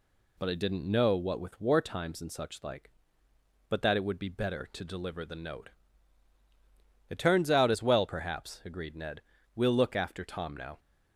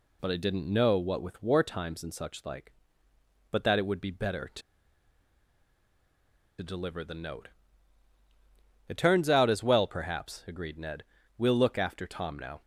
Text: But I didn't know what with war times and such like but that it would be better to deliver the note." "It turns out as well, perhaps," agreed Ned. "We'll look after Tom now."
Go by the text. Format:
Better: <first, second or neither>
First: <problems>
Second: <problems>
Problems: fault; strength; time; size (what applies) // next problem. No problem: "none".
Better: first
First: none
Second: pauses between "to" and "deliver"; strong; at 4.6 s; 1.9 s long